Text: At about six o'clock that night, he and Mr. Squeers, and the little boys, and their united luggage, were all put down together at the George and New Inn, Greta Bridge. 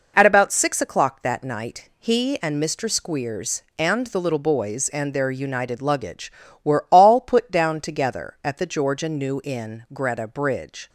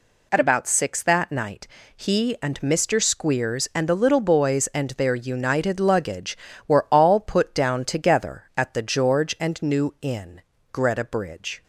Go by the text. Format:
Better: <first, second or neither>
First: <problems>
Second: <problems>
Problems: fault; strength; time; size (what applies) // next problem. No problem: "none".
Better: first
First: none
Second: skips "o'clock"; at 1.0 s